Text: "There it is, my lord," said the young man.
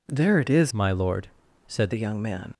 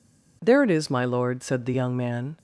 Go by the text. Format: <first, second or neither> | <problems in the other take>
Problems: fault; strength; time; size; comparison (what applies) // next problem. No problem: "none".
second | changes voice from "my" to "said"; from 0.7 to 1.9 s; 1.2 s long